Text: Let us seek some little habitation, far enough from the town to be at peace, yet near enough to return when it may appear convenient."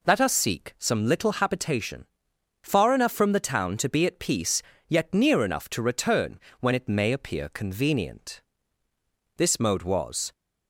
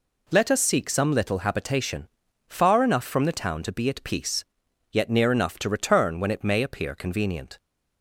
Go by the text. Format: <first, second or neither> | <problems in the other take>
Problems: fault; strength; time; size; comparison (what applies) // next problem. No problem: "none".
second | pauses between "return" and "when"; slight; at 6.3 s; 0.19 s long // goes on to say "This mode was"; noticeable; from 9.3 s on; 0.96 s long